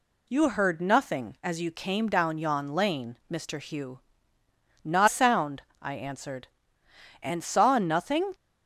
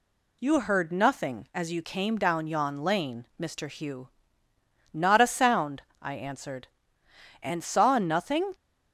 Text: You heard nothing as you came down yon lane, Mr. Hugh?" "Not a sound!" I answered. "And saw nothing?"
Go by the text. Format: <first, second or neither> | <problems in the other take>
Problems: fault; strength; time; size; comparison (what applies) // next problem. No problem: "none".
second | skips "a"; at 5.0 s